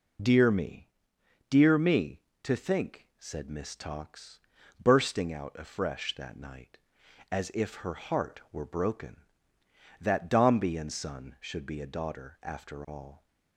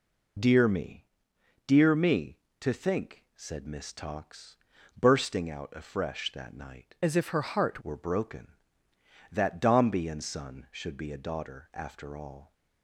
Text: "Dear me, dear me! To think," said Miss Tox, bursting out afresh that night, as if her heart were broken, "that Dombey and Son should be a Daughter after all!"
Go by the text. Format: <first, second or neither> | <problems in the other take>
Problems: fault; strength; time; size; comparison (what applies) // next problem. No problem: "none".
first | changes voice from "as" to "heart"; from 7.0 to 7.8 s; 0.8 s long